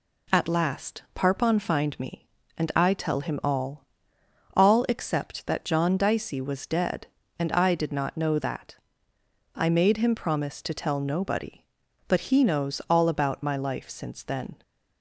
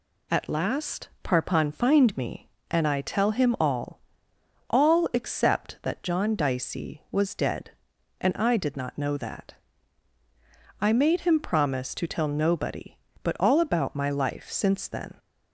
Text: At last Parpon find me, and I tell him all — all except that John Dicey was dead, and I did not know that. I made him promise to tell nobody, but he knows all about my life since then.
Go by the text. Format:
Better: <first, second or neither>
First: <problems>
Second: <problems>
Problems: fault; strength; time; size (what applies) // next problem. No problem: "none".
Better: first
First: none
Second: skips "he knows"; at 13.3 s